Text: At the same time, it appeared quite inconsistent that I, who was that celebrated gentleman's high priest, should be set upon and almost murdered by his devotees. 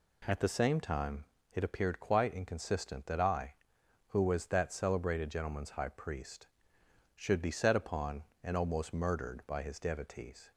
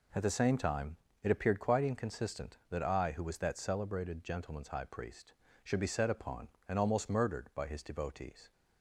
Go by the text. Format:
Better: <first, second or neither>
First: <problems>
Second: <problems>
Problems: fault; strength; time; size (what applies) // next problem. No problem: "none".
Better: neither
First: none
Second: none